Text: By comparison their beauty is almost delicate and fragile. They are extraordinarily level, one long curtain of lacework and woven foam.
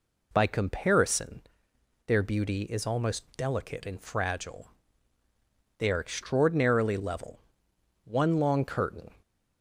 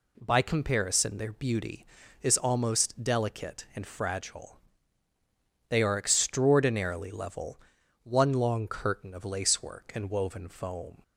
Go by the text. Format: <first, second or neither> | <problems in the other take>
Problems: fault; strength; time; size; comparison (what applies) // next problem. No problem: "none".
second | pauses between "comparison" and "their"; noticeable; at 1.4 s; 0.64 s long // stops before "of lacework and woven foam"; at 9.2 s